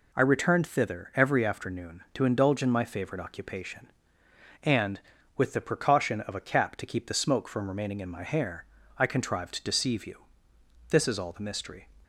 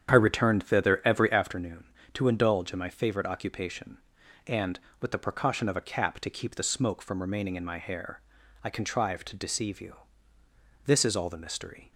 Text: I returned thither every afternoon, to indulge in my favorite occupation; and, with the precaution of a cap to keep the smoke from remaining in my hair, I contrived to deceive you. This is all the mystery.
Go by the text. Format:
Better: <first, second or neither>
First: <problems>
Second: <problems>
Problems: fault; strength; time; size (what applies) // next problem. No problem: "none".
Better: first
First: none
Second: starts louder than the rest; strong; until 1.6 s; 9 dB